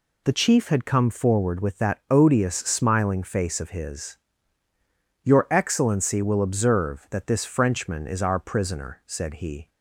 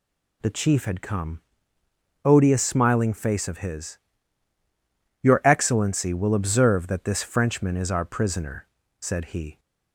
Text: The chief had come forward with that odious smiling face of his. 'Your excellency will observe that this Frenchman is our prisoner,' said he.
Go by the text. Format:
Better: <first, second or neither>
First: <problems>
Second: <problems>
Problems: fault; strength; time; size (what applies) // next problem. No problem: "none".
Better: first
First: none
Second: skips "forward with that"; at 1.8 s